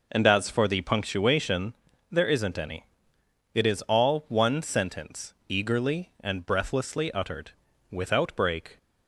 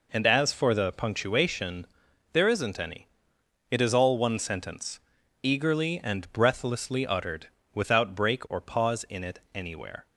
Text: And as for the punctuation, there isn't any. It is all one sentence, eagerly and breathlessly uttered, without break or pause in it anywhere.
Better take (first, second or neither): second